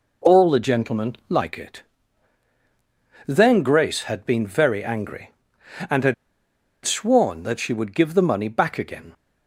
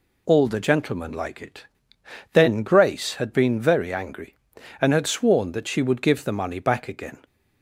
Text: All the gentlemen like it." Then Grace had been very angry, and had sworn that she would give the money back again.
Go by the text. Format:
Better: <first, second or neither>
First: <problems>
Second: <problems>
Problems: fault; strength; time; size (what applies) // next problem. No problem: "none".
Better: second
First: pauses between "had" and "sworn"; noticeable; at 6.1 s; 0.70 s long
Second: none